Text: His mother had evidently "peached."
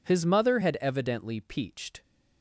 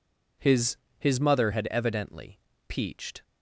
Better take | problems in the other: first | says "His" twice; at 1.0 s // pauses between "evidently" and "peached"; slight; at 2.3 s; 0.30 s long

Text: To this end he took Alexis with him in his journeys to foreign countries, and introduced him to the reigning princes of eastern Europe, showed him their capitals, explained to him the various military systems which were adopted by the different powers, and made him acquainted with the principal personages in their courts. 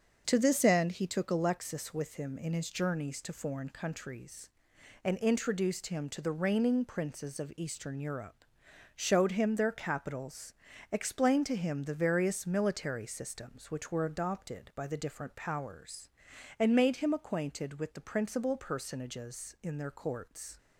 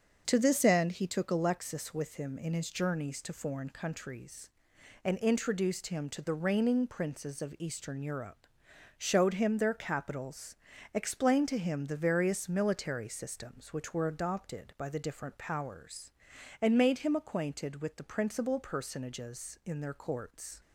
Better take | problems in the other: neither | starts louder than the rest; the same in both

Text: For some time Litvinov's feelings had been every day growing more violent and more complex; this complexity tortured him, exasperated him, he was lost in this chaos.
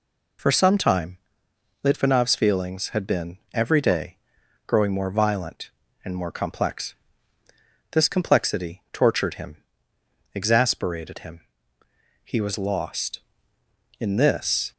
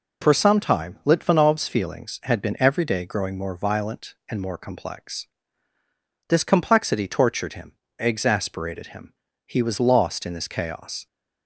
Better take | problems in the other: second | pauses between "time" and "Litvinov's"; noticeable; at 1.1 s; 0.66 s long // pauses between "been" and "every"; slight; at 3.3 s; 0.16 s long // pauses between "day" and "growing"; noticeable; at 4.1 s; 0.50 s long // stops before "chaos"; at 14.7 s

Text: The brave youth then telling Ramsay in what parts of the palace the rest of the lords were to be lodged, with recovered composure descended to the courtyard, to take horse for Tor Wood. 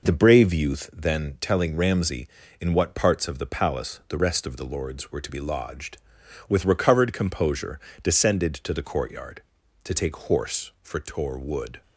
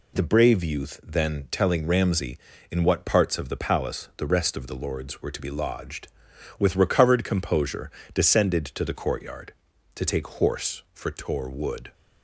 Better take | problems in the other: second | starts louder than the rest; noticeable; until 1.0 s; 5 dB // pauses between "composure" and "descended"; slight; at 7.7 s; 0.22 s long; slight in the second

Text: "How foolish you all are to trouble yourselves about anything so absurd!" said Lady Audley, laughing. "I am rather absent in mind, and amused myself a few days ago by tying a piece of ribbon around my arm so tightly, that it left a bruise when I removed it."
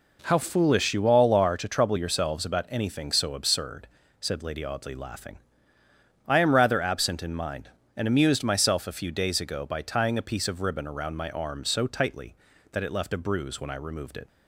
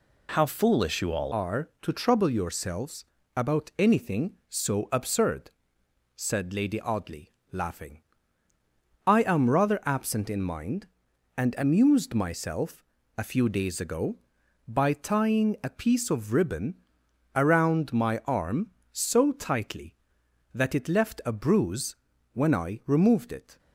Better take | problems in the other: first | changes voice at "are"; from 1.3 s on; 22.2 s long // pauses between "yourselves" and "about"; slight; at 3.0 s; 0.32 s long // pauses between "myself" and "a"; slight; at 12.8 s; 0.32 s long // pauses between "ribbon" and "around"; noticeable; at 16.8 s; 0.56 s long // pauses between "bruise" and "when"; at 21.9 s; 0.38 s long

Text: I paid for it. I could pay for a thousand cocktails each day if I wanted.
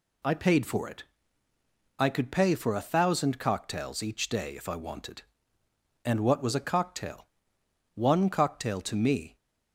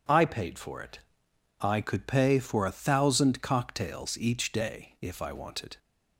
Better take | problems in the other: second | goes on to say "And what was a cocktail one cocktail to me"; strong; from 6.0 s on; 3.3 s long

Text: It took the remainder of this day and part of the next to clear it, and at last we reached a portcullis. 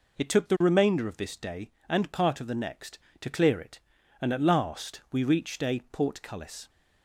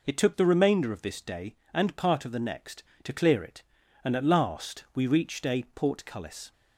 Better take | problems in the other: neither | none

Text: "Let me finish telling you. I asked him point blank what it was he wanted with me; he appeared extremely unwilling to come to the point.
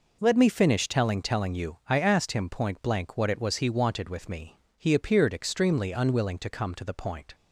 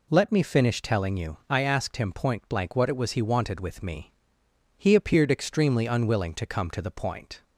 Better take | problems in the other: second | says "telling" twice; at 1.2 s

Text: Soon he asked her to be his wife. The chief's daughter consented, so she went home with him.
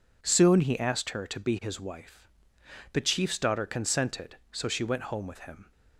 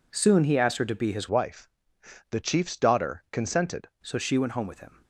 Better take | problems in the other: first | changes voice from "wife" to "consented"; from 1.2 to 3.8 s; 2.6 s long

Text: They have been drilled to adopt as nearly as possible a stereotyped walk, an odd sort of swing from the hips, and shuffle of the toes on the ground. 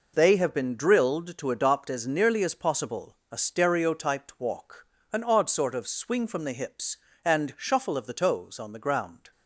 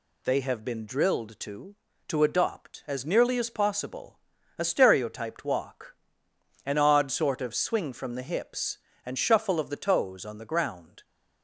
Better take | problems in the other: first | says "to" twice; at 2.0 s // pauses between "possible" and "a"; at 4.1 s; 0.40 s long; slight in the first

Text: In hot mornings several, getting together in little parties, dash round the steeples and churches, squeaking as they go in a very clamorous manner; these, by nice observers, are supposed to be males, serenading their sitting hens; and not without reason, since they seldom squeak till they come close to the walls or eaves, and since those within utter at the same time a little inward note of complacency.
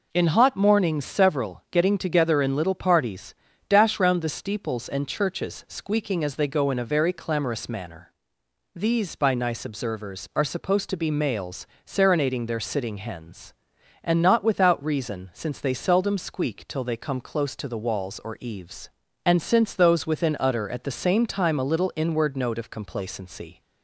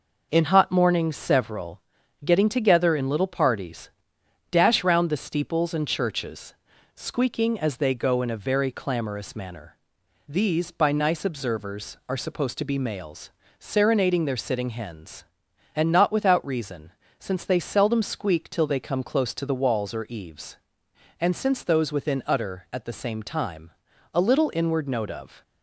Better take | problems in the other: first | pauses between "time" and "a"; at 23.7 s; 0.42 s long // stops before "complacency"; at 25.4 s

